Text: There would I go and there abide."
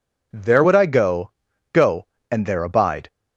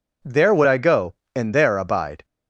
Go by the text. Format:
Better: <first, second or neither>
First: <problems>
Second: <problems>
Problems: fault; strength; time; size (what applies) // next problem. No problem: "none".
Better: second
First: says "go" twice; at 1.7 s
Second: none